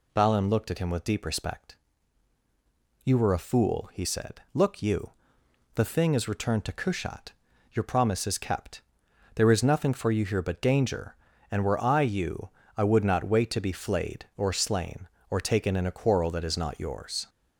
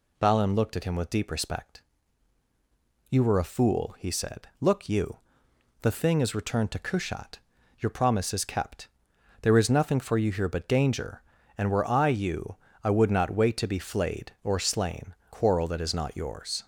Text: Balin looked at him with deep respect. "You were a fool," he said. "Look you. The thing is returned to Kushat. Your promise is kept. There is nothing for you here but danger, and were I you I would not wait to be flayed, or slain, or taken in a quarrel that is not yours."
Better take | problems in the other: first | pauses between "you" and "I"; slight; at 12.5 s; 0.28 s long; slight in the first // skips "or taken in a"; at 15.2 s

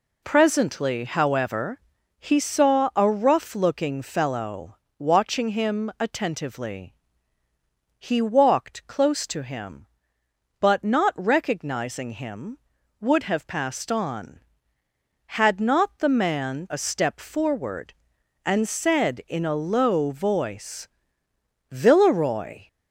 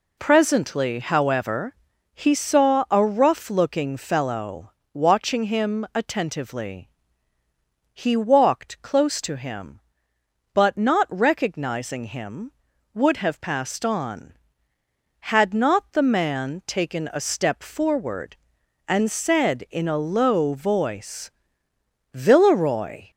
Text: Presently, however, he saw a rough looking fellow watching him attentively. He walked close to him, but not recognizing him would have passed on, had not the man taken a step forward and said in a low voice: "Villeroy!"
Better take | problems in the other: second | pauses between "fellow" and "watching"; slight; at 4.7 s; 0.20 s long; slight in the second // skips "taken"; at 16.6 s

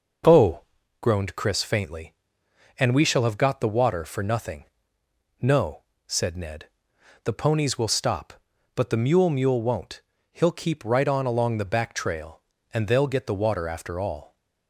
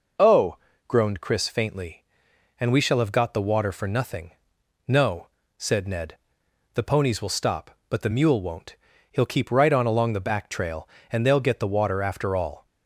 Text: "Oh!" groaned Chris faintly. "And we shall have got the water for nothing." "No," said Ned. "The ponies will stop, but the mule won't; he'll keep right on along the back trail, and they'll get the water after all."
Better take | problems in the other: second | says "mule" twice; at 9.2 s

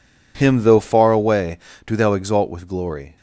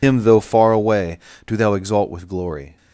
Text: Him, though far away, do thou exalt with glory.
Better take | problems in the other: first | loses the start of "Him"; at 0.0 s; 75 ms

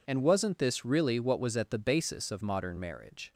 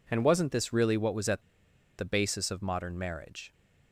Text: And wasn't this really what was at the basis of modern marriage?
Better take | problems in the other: first | pauses between "at" and "the"; noticeable; at 1.4 s; 0.56 s long

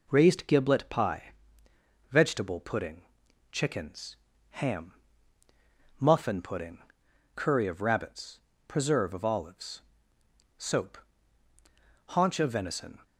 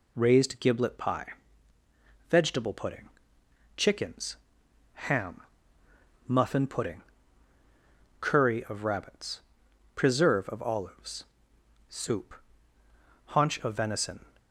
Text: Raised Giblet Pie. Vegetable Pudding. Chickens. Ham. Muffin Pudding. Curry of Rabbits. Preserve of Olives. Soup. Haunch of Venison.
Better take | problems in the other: second | says "Soap" for "Soup"; at 10.5 s

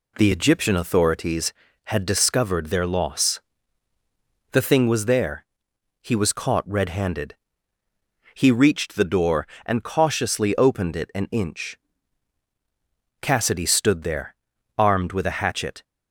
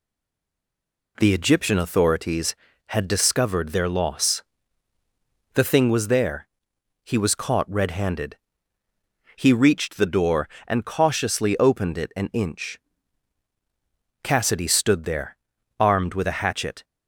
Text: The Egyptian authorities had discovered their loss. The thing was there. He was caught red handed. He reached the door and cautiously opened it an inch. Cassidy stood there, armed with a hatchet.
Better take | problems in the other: first | stays silent before the first word; until 1.1 s; 1.1 s long

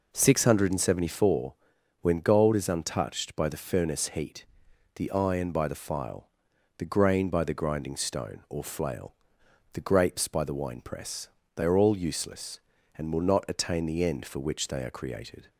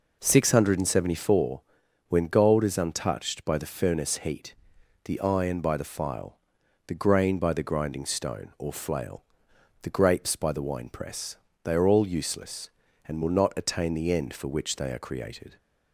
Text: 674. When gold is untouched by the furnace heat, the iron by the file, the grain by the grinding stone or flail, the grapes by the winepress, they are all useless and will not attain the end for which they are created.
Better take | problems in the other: neither | none

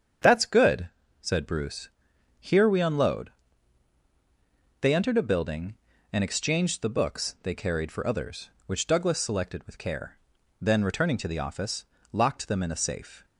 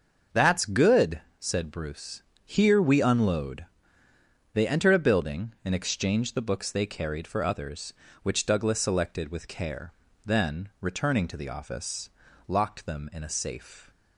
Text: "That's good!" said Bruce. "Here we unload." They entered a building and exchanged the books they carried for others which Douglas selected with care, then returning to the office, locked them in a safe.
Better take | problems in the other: neither | starts louder than the rest; the same in both

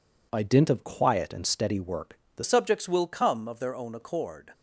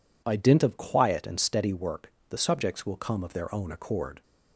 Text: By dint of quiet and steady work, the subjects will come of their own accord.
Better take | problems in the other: second | changes voice at "subjects"; from 2.4 s on; 2.1 s long

